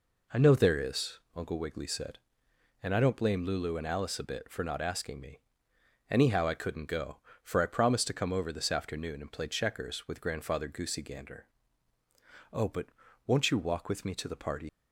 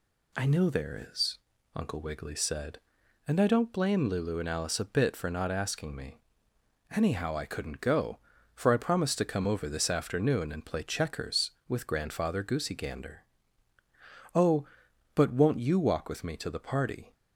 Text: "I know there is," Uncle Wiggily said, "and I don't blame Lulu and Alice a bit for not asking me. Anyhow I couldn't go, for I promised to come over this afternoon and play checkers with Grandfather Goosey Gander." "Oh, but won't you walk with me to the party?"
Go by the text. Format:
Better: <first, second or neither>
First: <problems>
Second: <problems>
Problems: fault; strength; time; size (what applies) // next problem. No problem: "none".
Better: second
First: pauses between "but" and "won't"; at 12.8 s; 0.38 s long // leaves "party" unfinished; at 14.6 s; 90 ms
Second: none